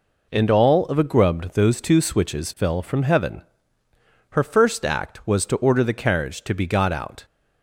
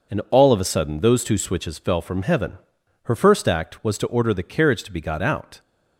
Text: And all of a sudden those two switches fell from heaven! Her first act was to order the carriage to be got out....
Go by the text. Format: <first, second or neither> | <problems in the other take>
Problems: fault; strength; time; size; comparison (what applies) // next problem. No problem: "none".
second | says "grubbed" for "sudden"; at 1.0 s